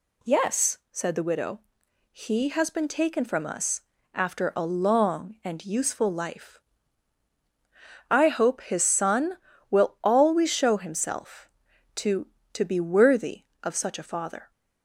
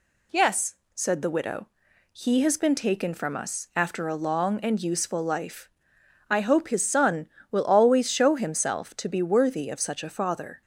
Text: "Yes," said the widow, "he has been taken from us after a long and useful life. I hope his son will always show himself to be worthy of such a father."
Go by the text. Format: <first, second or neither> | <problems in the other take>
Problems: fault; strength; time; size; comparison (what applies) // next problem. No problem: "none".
second | pauses between "us" and "after"; slight; at 3.8 s; 0.32 s long // says "to" twice; at 12.5 s